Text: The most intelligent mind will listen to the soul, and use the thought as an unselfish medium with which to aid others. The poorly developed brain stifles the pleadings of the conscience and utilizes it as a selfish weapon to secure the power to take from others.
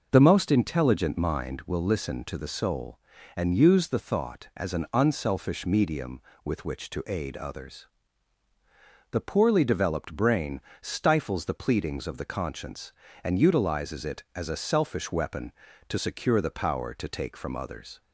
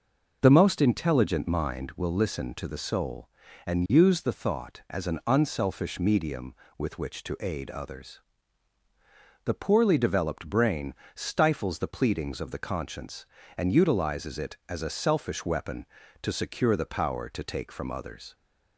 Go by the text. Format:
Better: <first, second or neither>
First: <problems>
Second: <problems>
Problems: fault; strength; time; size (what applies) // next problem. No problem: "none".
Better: neither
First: pauses between "brain" and "stifles"; slight; at 10.6 s; 0.20 s long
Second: pauses between "brain" and "stifles"; slight; at 10.9 s; 0.20 s long